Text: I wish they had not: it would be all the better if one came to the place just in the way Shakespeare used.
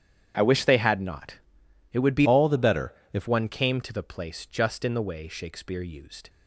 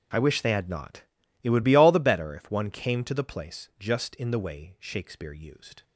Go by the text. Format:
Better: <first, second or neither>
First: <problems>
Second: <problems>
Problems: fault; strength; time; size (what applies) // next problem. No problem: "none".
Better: second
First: starts louder than the rest; strong; until 1.3 s; 9 dB // changes voice from "all" to "if"; from 2.2 to 3.2 s; 1.0 s long // pauses between "better" and "if"; slight; at 2.9 s; 0.20 s long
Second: starts louder than the rest; until 1.5 s; 7 dB